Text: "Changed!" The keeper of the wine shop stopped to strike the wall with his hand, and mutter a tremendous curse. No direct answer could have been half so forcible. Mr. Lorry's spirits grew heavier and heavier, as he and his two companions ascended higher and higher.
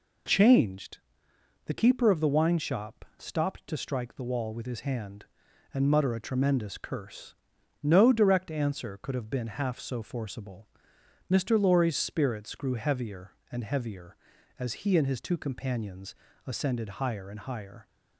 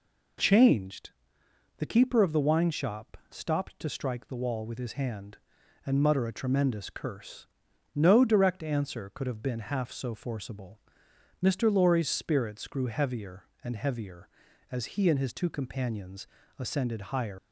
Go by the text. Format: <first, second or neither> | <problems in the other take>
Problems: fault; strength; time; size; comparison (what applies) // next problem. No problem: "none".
first | pauses between "companions" and "ascended"; slight; at 16.2 s; 0.32 s long; slight in the first // stops before "and higher"; at 17.3 s